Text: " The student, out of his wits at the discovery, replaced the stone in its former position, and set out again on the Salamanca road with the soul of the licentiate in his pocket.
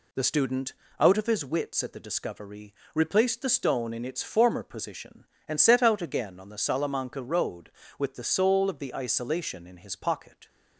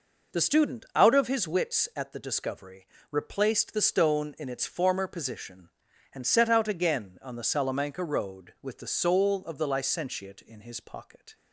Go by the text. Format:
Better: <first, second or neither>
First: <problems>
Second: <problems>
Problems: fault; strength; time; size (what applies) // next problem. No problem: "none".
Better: second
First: says "isolation" for "licentiate"; at 8.9 s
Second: none